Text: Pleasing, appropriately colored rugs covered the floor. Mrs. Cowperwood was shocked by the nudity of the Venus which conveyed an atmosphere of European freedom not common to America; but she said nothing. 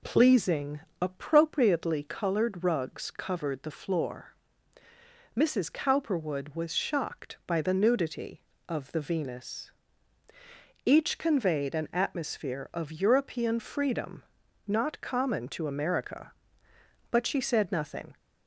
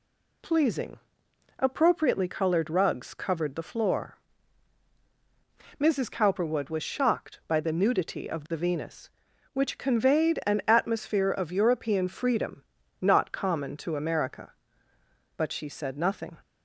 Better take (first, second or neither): second